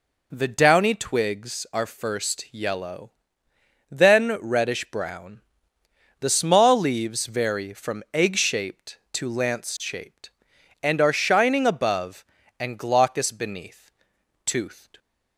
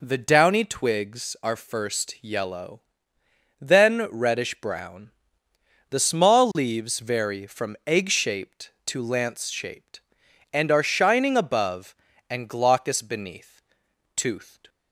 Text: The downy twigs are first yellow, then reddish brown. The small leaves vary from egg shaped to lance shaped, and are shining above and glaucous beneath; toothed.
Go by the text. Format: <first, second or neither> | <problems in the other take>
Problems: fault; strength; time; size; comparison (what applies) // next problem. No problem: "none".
neither | none